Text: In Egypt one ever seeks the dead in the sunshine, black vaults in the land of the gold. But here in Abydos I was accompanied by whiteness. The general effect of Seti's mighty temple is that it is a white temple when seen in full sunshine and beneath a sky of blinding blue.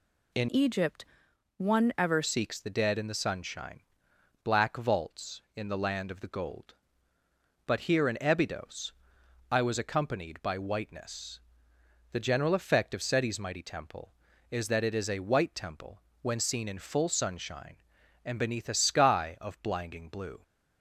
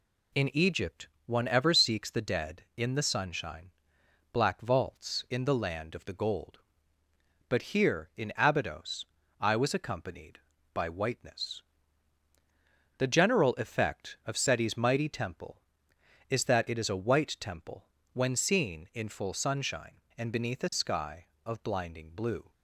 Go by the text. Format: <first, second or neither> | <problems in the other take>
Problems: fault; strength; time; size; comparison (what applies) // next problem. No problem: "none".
second | changes voice from "Egypt" to "ever"; from 0.4 to 2.2 s; 1.8 s long // pauses between "Egypt" and "one"; noticeable; at 1.0 s; 0.52 s long; slight in the second // pauses between "Abydos" and "I"; noticeable; at 8.9 s; 0.58 s long; slight in the second // pauses between "temple" and "when"; slight; at 16.0 s; 0.22 s long; slight in the second